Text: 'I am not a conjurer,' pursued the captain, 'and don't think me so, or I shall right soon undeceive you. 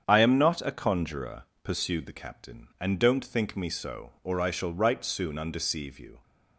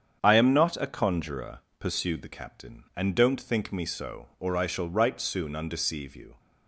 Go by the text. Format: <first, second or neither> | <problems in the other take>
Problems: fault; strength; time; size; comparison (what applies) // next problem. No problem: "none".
neither | starts louder than the rest; strong; the same in both